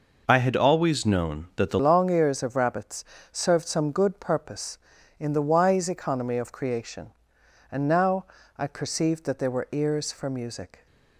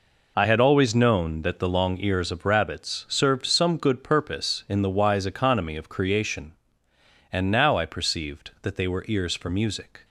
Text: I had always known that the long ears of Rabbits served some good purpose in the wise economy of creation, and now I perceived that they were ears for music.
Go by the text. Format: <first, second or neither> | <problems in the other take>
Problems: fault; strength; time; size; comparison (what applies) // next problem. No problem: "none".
second | changes voice at "long"; from 1.8 s on; 9.0 s long // pauses between "Rabbits" and "served"; slight; at 3.0 s; 0.28 s long // pauses between "now" and "I"; slight; at 8.2 s; 0.32 s long